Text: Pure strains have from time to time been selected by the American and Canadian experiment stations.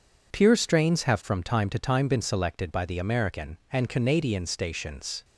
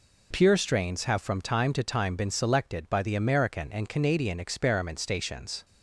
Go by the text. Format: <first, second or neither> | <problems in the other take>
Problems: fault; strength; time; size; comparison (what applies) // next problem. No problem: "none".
second | skips "experiment"; at 4.4 s